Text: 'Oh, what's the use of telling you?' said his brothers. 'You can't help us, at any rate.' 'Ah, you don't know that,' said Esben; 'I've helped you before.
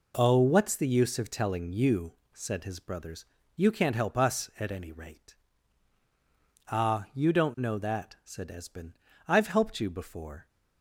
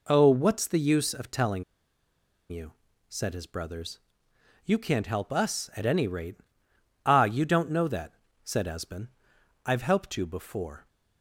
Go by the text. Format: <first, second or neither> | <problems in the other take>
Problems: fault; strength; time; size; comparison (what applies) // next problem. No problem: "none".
first | pauses between "telling" and "you"; noticeable; at 1.6 s; 0.86 s long